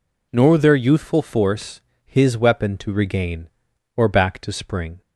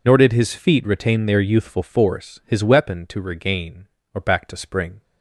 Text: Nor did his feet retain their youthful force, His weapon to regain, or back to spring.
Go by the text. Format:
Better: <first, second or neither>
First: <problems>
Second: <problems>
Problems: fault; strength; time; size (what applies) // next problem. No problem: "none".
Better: second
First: skips "did his feet retain"; at 0.5 s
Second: none